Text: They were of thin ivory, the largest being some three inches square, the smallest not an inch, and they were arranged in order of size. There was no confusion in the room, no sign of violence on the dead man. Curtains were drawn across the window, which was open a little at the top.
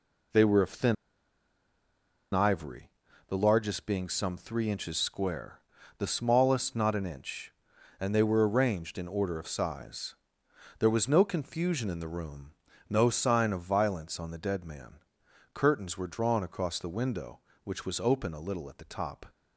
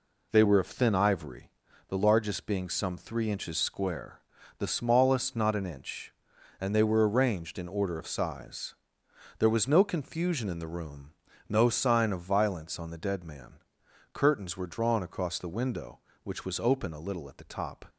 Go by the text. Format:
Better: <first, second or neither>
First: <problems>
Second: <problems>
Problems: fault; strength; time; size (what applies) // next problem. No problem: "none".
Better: second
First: pauses between "thin" and "ivory"; strong; at 0.9 s; 1.3 s long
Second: none